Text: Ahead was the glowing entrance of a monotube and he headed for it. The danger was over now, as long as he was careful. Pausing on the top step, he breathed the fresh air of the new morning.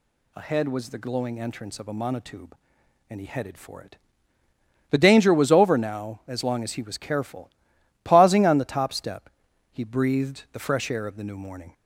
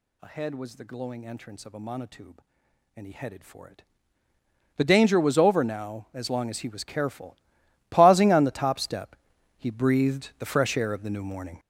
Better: first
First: none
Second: gets louder; strong; throughout; 11 dB

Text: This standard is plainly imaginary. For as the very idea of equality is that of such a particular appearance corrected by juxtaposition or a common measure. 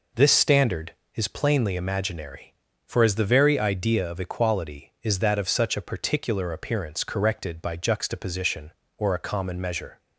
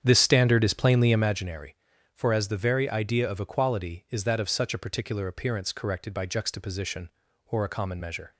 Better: first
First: none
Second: starts louder than the rest; strong; until 1.5 s; 8.5 dB

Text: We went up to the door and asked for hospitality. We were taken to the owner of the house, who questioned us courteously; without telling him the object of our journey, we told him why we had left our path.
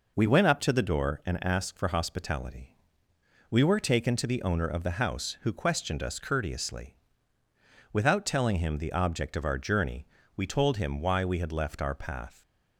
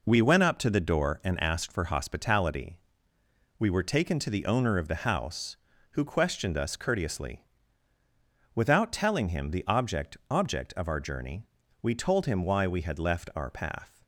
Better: first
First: none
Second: says "object" twice; at 10.2 s

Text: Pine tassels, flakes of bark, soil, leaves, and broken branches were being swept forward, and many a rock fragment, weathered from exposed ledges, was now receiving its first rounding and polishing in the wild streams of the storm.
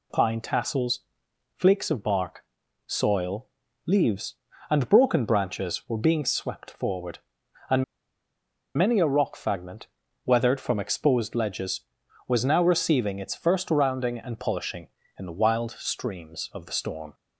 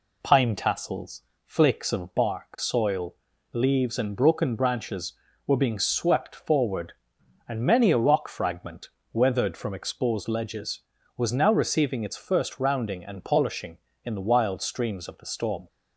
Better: second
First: pauses between "and" and "many"; noticeable; at 7.8 s; 0.93 s long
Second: none

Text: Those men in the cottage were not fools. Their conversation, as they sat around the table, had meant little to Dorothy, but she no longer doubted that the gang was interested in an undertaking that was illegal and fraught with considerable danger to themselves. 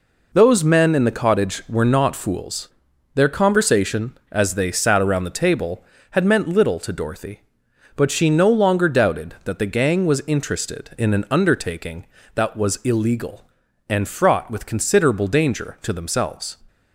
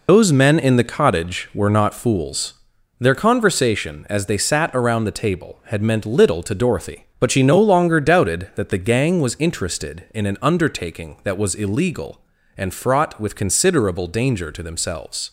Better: first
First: none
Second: loses the start of "Those"; at 0.0 s; 115 ms

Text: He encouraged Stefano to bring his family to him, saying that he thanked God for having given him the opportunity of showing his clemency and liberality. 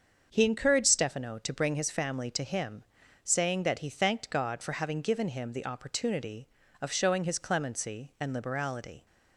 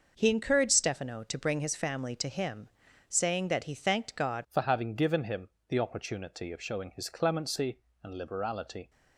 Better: first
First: starts louder than the rest; until 1.3 s; 7 dB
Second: starts louder than the rest; noticeable; until 1.1 s; 6 dB // changes voice at "for"; from 4.4 s on; 4.4 s long // pauses between "him" and "the"; slight; at 5.4 s; 0.18 s long

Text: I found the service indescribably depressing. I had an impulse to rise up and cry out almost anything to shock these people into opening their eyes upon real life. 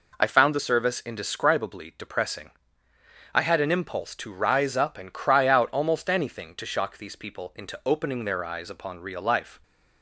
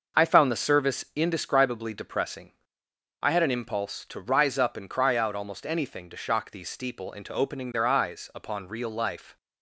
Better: first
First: none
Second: starts louder than the rest; noticeable; until 1.3 s; 6 dB // says "steeple" for "people"; at 6.6 s

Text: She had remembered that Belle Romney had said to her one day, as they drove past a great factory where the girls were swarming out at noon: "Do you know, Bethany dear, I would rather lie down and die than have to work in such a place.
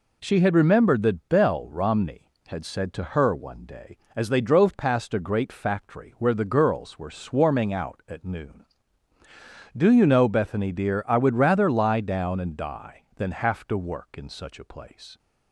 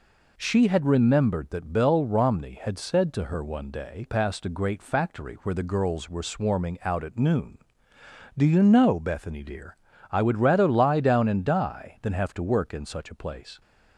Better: first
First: none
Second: skips "as they drove"; at 4.0 s

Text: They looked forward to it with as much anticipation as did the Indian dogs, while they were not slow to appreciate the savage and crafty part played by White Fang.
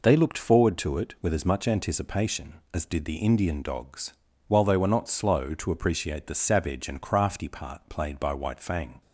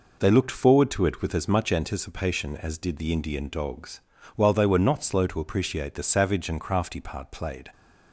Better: first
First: none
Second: stops before "by White Fang"; at 7.7 s

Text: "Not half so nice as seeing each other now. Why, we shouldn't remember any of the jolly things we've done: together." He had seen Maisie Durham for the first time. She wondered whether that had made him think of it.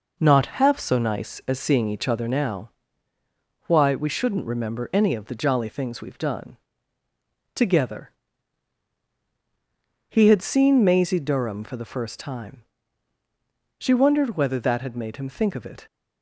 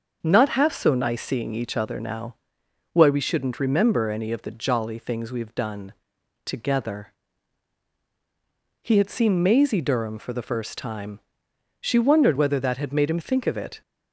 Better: first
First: none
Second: starts louder than the rest; until 1.2 s; 6.5 dB // skips "as"; at 1.2 s

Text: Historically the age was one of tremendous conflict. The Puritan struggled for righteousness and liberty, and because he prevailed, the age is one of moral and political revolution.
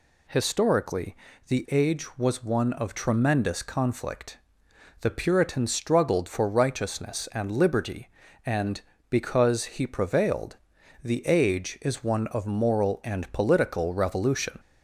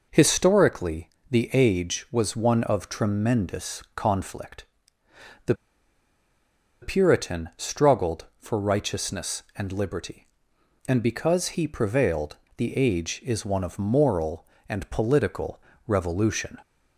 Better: first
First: pauses between "Historically" and "the"; slight; at 1.1 s; 0.32 s long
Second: pauses between "Historically" and "the"; slight; at 1.0 s; 0.22 s long // pauses between "The" and "Puritan"; strong; at 5.5 s; 1.2 s long // pauses between "political" and "revolution"; slight; at 15.5 s; 0.28 s long

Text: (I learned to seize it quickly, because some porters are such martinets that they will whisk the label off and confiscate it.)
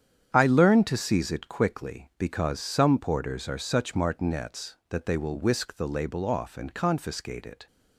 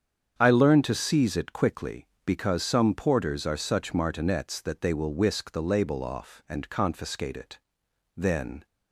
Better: first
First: starts louder than the rest; strong; until 1.3 s; 8.5 dB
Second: starts louder than the rest; strong; until 1.4 s; 8 dB // goes on to say "Then"; slight; from 8.1 s on; 0.48 s long

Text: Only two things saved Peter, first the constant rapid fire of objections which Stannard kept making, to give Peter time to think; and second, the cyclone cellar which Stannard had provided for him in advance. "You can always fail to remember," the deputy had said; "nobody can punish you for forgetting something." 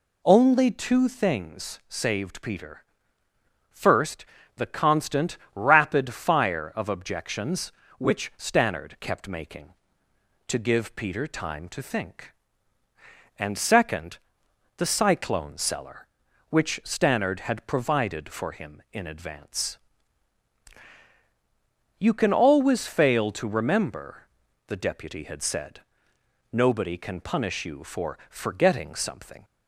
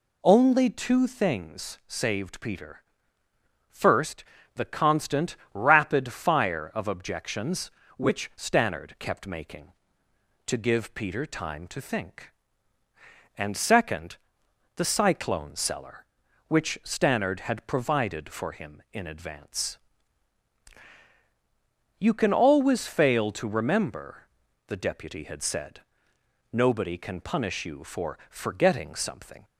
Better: neither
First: pauses between "first" and "the"; slight; at 4.2 s; 0.30 s long // pauses between "constant" and "rapid"; slight; at 5.3 s; 0.16 s long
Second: pauses between "first" and "the"; slight; at 4.2 s; 0.30 s long // pauses between "constant" and "rapid"; slight; at 5.3 s; 0.16 s long

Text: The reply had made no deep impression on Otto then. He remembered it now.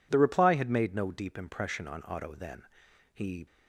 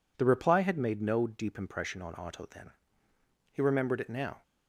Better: second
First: stops before "remembered it now"; at 3.4 s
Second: none

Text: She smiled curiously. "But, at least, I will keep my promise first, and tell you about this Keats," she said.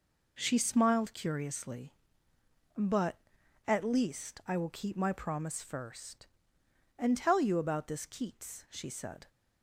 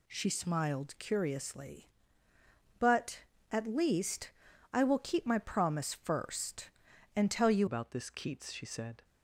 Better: first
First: none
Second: changes voice at "about"; from 7.6 s on; 1.4 s long

